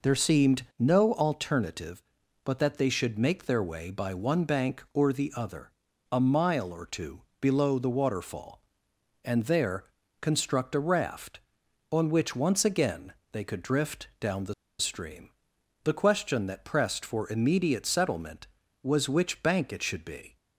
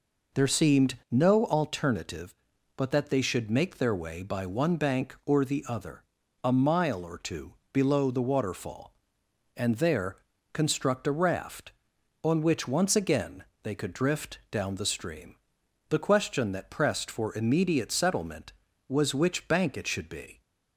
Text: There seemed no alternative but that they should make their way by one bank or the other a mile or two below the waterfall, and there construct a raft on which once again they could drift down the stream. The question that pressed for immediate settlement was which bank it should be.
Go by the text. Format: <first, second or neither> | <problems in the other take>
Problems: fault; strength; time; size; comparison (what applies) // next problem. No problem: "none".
second | pauses between "seemed" and "no"; slight; at 0.6 s; 0.16 s long; slight in the second // pauses between "other" and "a"; at 5.6 s; 0.42 s long; also in the second // pauses between "two" and "below"; slight; at 7.2 s; 0.18 s long; slight in the second // pauses between "there" and "construct"; slight; at 9.8 s; 0.36 s long; slight in the second // pauses between "again" and "they"; slight; at 13.1 s; 0.18 s long; slight in the second // pauses between "the" and "stream"; slight; at 14.5 s; 0.27 s long